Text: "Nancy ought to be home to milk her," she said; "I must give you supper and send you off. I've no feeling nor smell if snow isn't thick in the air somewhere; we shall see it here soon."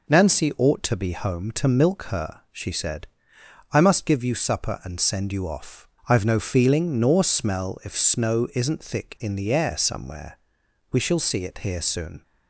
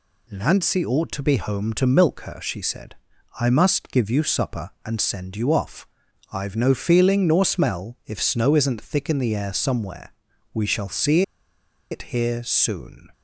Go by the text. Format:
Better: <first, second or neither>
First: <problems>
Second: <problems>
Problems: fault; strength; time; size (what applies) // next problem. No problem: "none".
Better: first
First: none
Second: pauses between "see" and "it"; noticeable; at 11.2 s; 0.69 s long